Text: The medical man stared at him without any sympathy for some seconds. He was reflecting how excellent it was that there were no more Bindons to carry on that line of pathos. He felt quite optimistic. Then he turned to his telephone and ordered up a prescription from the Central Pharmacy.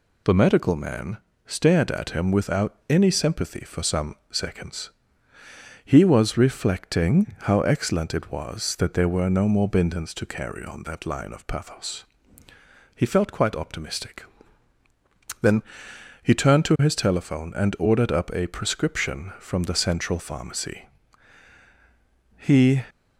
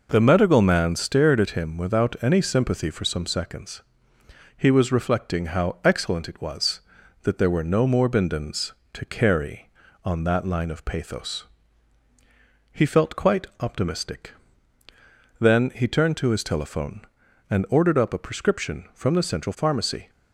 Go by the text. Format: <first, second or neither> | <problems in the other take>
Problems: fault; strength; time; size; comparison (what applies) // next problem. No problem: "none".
second | pauses between "man" and "stared"; slight; at 1.1 s; 0.30 s long // pauses between "some" and "seconds"; slight; at 4.1 s; 0.16 s long // pauses between "Then" and "he"; noticeable; at 15.6 s; 0.62 s long // goes on to say "He"; slight; from 22.3 s on; 0.46 s long